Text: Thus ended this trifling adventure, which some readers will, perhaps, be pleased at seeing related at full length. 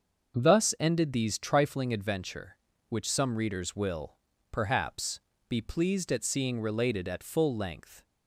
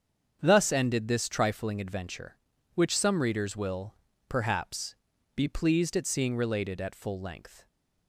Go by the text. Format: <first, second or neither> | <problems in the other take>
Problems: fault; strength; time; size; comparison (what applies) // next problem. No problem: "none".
second | starts louder than the rest; until 1.4 s; 6.5 dB; strong in the second // says "these" for "this"; at 1.1 s